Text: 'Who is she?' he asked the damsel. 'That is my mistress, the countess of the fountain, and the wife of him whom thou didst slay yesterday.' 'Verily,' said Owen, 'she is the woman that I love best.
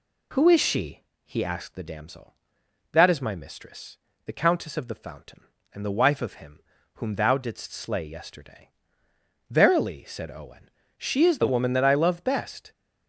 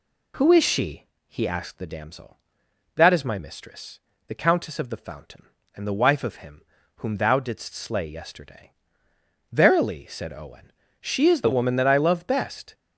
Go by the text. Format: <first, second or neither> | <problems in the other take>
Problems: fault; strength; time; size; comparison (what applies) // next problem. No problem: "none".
neither | pauses between "him" and "whom"; slight; the same in both